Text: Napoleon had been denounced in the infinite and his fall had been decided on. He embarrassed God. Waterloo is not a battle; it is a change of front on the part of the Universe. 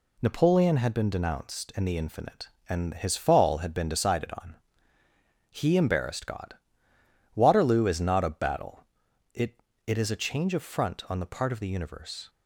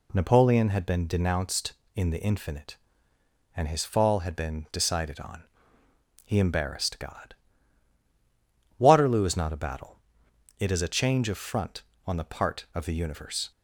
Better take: second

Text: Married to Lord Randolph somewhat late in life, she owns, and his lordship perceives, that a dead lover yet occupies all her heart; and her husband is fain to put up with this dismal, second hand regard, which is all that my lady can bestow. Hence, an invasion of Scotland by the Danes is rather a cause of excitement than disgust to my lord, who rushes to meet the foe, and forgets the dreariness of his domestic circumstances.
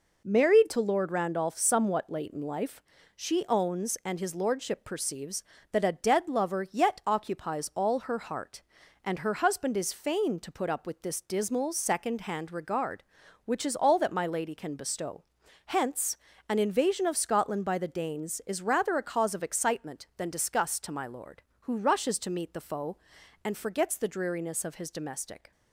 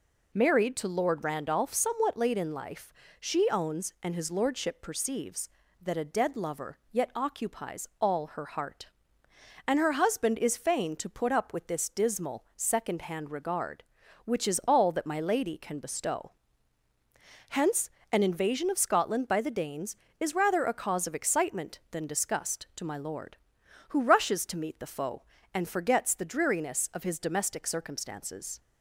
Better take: second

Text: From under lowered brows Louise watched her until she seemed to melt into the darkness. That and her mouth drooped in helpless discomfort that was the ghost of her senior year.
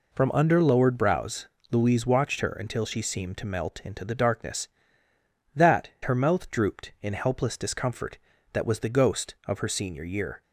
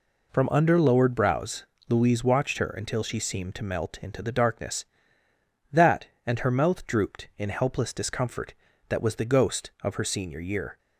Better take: second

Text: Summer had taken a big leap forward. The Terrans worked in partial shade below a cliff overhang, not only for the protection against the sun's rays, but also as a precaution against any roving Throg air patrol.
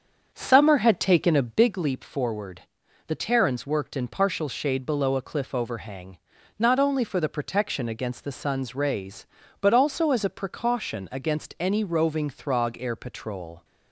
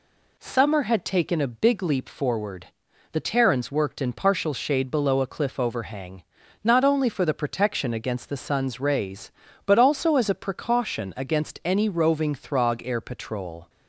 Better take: second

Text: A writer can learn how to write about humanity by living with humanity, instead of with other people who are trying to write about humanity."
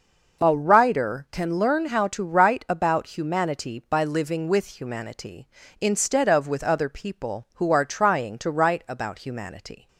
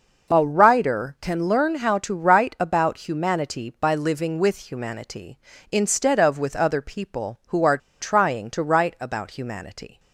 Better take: first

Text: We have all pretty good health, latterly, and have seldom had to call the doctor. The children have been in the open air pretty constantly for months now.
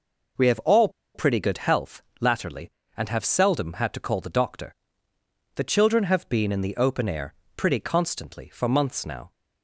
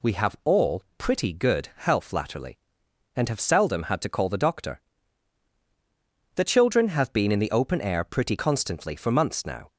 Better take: second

